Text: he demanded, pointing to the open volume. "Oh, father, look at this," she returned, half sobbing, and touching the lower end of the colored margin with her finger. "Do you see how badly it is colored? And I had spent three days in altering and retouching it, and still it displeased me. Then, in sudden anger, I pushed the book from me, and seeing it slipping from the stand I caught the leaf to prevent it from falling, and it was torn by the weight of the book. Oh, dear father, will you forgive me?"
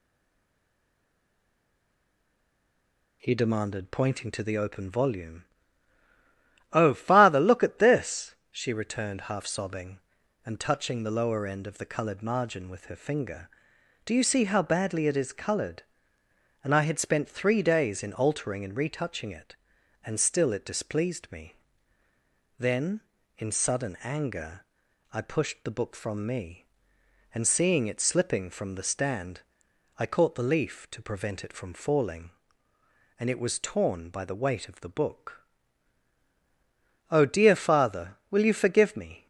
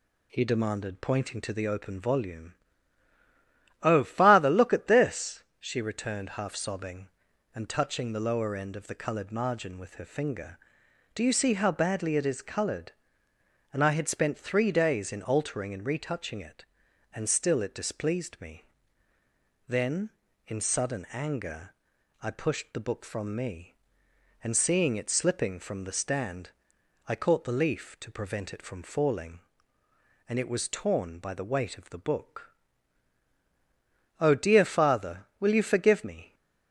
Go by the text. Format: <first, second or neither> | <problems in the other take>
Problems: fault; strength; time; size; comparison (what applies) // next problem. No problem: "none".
second | stays silent before the first word; strong; until 3.2 s; 3.2 s long // pauses between "stand" and "I"; noticeable; at 29.4 s; 0.56 s long; noticeable in the second